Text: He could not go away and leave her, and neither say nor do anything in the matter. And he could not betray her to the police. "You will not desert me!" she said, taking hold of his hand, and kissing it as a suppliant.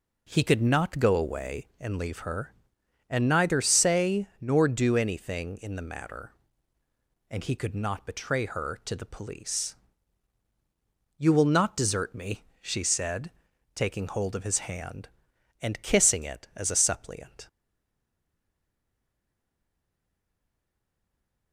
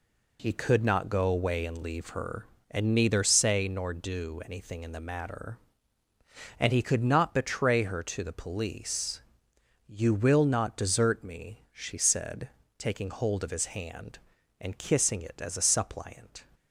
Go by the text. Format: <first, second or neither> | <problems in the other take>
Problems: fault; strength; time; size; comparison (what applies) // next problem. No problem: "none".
second | stays silent after the last word; strong; from 17.4 s on; 4.1 s long